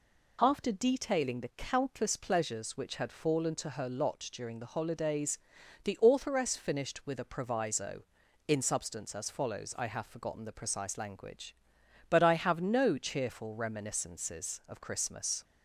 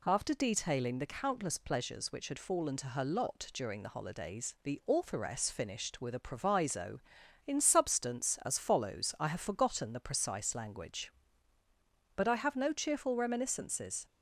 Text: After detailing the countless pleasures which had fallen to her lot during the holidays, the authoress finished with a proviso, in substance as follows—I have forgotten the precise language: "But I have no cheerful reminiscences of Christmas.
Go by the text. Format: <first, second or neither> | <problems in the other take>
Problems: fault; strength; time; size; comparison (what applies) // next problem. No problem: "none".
first | stops before "of Christmas"; at 14.0 s